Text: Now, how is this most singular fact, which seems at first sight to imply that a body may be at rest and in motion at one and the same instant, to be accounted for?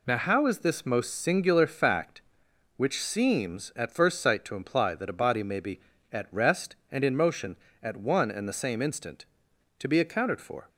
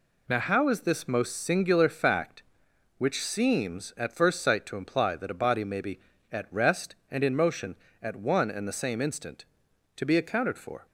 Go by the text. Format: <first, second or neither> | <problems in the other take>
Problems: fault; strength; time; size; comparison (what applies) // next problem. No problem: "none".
neither | none